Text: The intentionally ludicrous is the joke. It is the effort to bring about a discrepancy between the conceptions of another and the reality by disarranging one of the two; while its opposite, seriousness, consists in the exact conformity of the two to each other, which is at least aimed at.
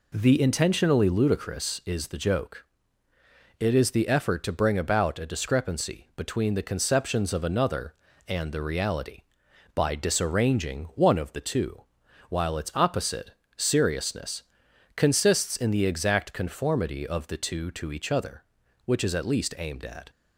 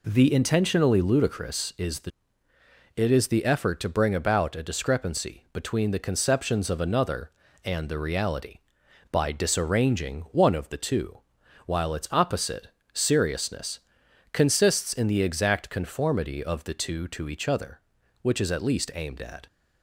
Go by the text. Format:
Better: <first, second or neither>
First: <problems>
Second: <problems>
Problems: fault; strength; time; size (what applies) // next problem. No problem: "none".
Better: first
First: none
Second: skips "joke"; at 2.5 s